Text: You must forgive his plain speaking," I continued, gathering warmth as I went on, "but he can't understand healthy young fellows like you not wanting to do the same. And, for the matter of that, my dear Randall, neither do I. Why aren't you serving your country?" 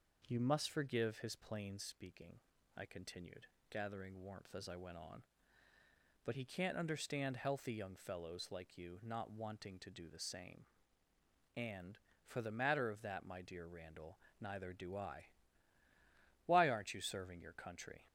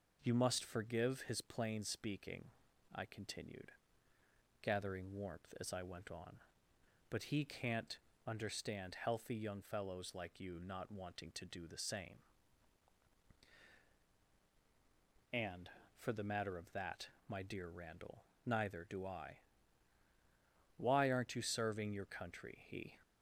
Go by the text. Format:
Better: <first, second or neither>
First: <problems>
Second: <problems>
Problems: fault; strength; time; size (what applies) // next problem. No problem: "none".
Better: first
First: none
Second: pauses between "can't" and "understand"; slight; at 7.9 s; 0.30 s long // goes on to say "He"; slight; from 22.6 s on; 0.32 s long